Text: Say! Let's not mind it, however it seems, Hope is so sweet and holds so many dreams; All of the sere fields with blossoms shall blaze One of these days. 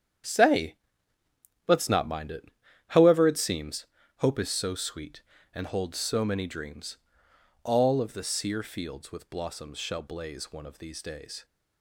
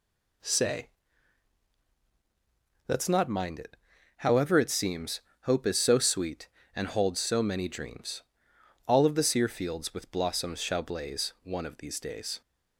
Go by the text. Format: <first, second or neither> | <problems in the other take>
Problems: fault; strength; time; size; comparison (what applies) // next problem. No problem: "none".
second | gets quieter; strong; throughout; 11.5 dB